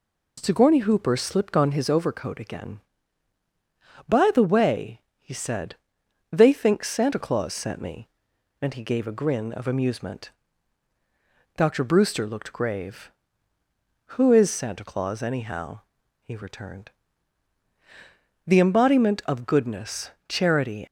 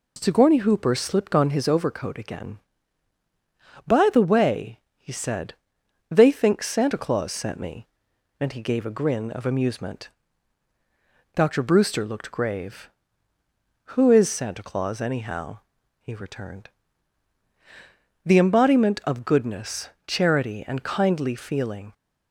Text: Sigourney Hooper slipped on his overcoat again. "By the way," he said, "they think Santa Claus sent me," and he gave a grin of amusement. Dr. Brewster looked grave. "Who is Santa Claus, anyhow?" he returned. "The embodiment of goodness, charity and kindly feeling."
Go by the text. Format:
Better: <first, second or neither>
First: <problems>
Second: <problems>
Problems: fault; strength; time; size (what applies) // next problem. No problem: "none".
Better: second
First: stops before "and kindly feeling"; at 20.8 s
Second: none